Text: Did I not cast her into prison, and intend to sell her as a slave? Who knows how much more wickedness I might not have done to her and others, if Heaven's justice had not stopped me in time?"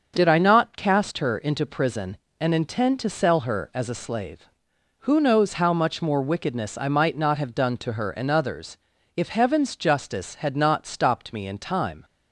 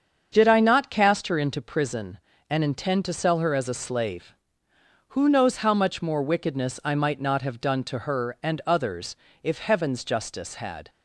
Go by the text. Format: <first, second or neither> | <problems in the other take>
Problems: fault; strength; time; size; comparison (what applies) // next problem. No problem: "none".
first | starts louder than the rest; until 1.3 s; 7 dB; also in the first // stops before "not stopped me in time"; at 10.8 s